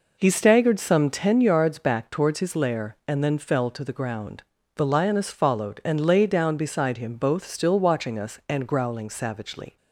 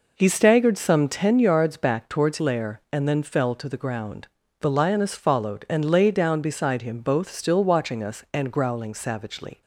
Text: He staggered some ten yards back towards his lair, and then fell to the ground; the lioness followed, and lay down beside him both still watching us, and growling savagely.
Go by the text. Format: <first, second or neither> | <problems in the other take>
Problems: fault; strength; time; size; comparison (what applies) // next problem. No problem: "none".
first | skips "his"; at 2.3 s